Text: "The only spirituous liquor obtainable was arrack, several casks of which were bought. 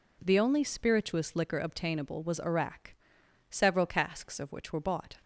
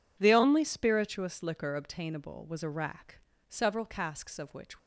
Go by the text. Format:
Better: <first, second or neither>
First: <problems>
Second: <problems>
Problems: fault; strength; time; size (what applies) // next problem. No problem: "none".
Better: first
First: none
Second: stops before "were bought"; at 4.7 s